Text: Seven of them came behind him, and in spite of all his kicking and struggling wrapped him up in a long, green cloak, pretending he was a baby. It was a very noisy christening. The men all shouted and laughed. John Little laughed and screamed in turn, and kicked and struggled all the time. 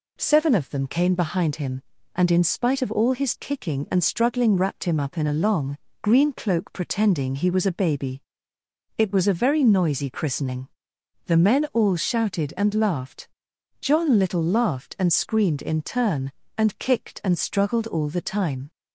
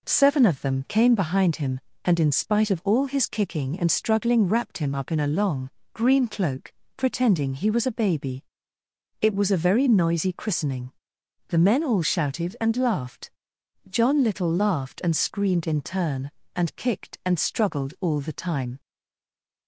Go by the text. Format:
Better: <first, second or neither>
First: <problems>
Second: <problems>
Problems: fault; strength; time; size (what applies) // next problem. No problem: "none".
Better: first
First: none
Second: stays silent after the last word; slight; from 18.7 s on; 0.9 s long